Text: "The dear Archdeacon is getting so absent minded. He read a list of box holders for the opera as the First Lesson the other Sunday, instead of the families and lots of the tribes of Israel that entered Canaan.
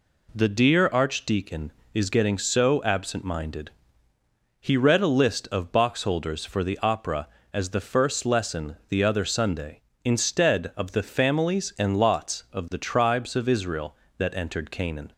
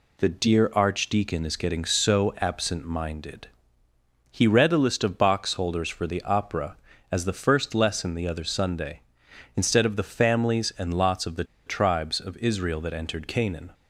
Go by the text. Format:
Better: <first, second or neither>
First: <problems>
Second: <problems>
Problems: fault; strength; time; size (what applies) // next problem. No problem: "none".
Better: first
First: none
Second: pauses between "the" and "tribes"; slight; at 11.4 s; 0.22 s long